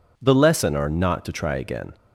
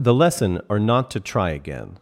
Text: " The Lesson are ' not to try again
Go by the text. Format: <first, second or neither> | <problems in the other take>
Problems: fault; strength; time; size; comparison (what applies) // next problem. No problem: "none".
neither | none